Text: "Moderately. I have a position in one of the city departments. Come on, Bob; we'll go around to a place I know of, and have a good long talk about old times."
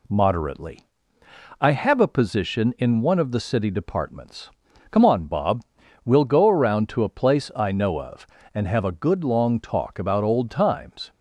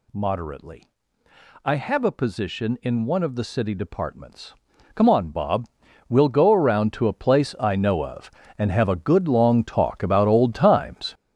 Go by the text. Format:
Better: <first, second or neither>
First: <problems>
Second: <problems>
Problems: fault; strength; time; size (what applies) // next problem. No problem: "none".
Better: first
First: none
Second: gets louder; strong; throughout; 8 dB